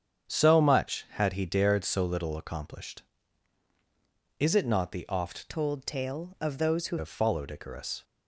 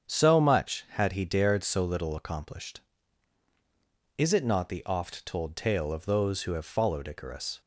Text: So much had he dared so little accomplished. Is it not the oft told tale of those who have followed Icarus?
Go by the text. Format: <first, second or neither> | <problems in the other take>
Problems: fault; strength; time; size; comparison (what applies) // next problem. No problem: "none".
second | starts louder than the rest; strong; until 1.3 s; 8 dB; strong in the second // changes voice from "told" to "who"; from 5.4 to 6.9 s; 1.5 s long